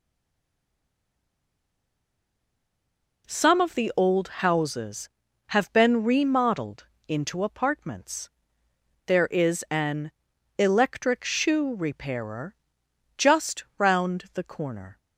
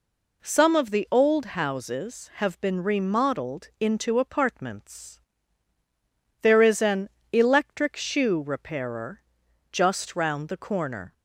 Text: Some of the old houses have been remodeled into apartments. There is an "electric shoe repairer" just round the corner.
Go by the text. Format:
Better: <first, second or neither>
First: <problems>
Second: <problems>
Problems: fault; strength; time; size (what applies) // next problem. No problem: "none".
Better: second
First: stays silent before the first word; strong; until 3.2 s; 3.2 s long // pauses between "remodeled" and "into"; slight; at 6.8 s; 0.22 s long // pauses between "an" and "electric"; noticeable; at 10.1 s; 0.48 s long // pauses between "repairer" and "just"; noticeable; at 12.5 s; 0.64 s long // pauses between "just" and "round"; slight; at 13.6 s; 0.16 s long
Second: pauses between "an" and "electric"; slight; at 7.0 s; 0.22 s long // pauses between "repairer" and "just"; noticeable; at 9.2 s; 0.50 s long